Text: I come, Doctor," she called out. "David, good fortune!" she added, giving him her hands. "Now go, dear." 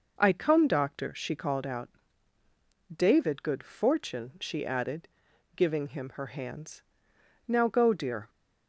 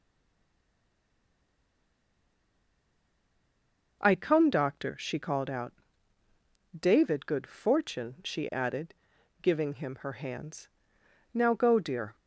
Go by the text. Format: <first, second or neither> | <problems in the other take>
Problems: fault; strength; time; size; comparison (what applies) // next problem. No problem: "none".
first | stays silent before the first word; strong; until 4.0 s; 4.0 s long